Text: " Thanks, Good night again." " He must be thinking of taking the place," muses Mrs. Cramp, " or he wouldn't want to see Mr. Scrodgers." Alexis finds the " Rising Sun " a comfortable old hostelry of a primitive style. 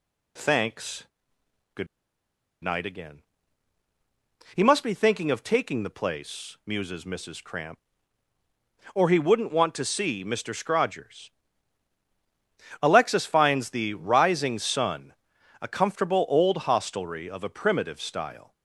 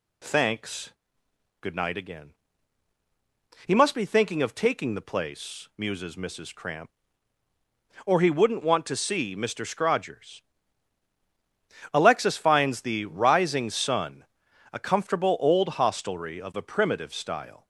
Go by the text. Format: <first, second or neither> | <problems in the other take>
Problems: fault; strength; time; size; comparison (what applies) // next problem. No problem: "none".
second | pauses between "Good" and "night"; noticeable; at 1.8 s; 0.76 s long